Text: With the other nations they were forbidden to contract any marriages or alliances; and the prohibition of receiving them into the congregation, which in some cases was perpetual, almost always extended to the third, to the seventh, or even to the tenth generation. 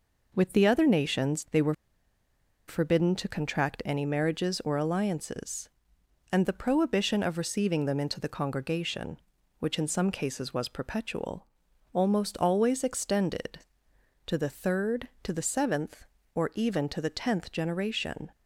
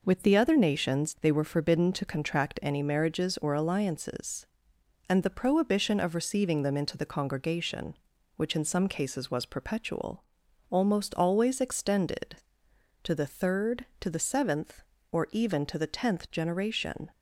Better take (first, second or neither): second